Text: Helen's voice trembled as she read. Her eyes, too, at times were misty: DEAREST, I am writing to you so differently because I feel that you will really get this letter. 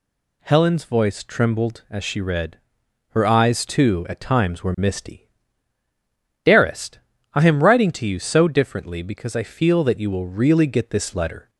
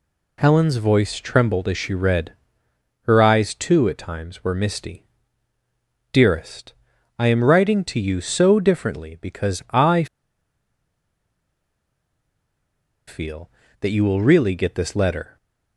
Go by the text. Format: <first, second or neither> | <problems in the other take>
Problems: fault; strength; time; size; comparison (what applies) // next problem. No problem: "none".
first | pauses between "I" and "feel"; strong; at 10.0 s; 3.0 s long